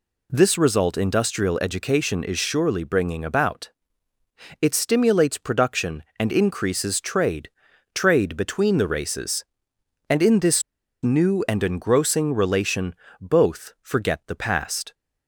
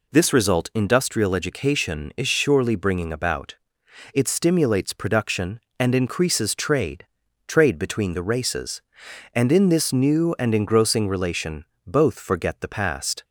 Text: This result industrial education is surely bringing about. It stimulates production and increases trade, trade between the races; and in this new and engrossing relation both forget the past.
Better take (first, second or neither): second